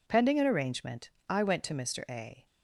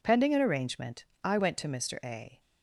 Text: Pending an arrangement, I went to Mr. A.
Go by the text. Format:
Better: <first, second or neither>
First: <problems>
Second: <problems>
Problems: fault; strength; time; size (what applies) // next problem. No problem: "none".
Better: neither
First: none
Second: none